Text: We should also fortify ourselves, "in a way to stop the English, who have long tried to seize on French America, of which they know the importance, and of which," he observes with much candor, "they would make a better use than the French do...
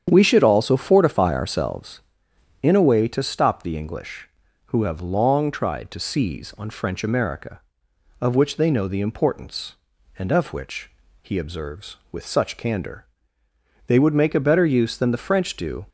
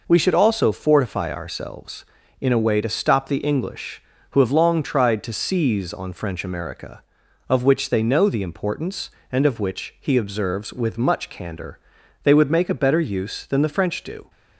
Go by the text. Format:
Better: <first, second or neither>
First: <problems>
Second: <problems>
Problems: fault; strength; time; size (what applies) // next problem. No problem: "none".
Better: second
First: starts louder than the rest; strong; until 1.0 s; 8.5 dB // says "such" for "much"; at 12.2 s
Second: none